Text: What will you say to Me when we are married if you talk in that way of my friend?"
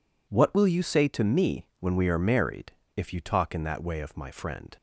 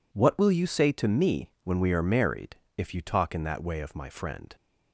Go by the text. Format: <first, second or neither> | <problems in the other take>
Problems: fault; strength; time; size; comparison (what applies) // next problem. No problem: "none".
neither | pauses between "married" and "if"; slight; the same in both